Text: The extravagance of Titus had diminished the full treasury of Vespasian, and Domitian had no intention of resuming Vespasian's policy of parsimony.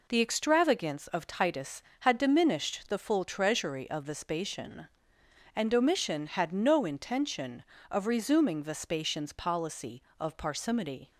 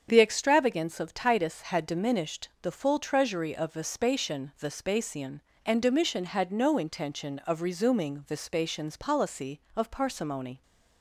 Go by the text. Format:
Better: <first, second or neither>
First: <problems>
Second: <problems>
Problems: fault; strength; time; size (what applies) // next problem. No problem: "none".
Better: first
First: none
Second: starts louder than the rest; strong; until 1.1 s; 7.5 dB // pauses between "diminished" and "the"; slight; at 2.4 s; 0.16 s long // says "Vespasian" twice; at 4.5 s